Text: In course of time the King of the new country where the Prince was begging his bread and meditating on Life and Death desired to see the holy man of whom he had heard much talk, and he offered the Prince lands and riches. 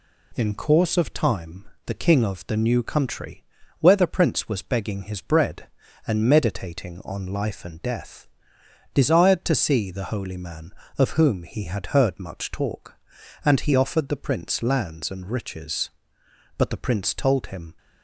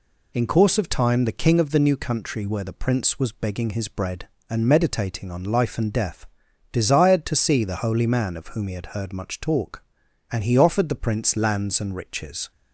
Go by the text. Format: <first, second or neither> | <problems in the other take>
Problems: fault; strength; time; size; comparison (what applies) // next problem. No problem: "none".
second | pauses between "time" and "the"; slight; at 1.6 s; 0.20 s long // pauses between "country" and "where"; at 3.4 s; 0.38 s long // pauses between "Death" and "desired"; noticeable; at 8.2 s; 0.68 s long; also in the second // goes on to say "But the Prince told him"; noticeable; from 16.5 s on; 1.1 s long